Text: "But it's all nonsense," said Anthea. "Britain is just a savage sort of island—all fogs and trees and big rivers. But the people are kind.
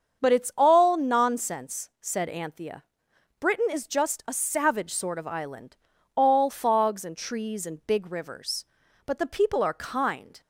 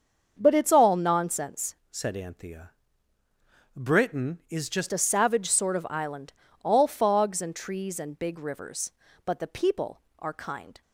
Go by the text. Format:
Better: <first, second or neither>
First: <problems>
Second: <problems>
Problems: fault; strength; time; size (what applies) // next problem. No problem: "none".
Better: first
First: starts louder than the rest; until 1.2 s; 7 dB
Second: starts louder than the rest; until 1.3 s; 6.5 dB // changes voice from "said" to "just"; from 1.9 to 4.8 s; 2.9 s long